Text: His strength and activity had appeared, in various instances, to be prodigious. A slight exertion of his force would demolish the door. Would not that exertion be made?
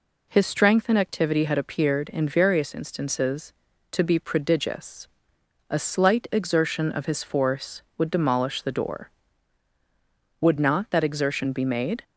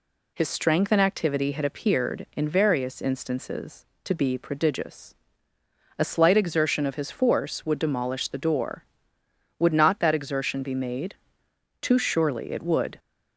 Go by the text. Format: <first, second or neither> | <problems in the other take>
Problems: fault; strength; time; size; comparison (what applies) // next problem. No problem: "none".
first | goes on to say "Too surely it would"; noticeable; from 11.8 s on; 1.1 s long